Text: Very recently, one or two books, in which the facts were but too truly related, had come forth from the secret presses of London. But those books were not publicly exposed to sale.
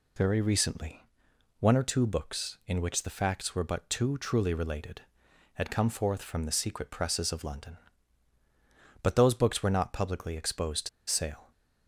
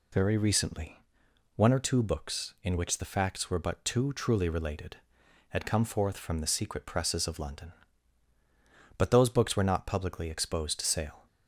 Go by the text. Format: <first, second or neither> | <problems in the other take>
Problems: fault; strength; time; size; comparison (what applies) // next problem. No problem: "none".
second | pauses between "to" and "sale"; slight; at 10.8 s; 0.19 s long